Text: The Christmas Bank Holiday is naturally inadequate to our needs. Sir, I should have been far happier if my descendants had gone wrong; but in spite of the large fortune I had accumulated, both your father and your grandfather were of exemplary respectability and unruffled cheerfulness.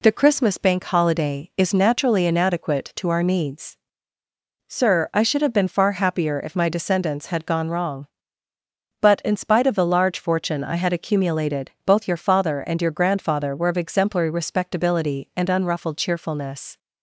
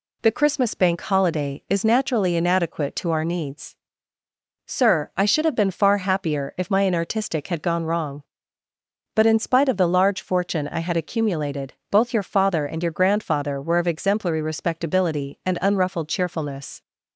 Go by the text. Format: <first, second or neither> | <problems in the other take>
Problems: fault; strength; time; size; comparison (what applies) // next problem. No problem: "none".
first | says "inartistic" for "descendants"; at 6.8 s